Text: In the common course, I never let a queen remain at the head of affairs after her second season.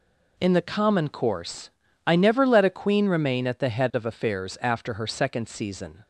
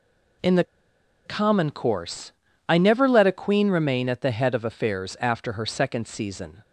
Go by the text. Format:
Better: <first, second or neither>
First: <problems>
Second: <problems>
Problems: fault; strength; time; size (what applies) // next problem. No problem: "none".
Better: first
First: none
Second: pauses between "the" and "common"; noticeable; at 0.6 s; 0.62 s long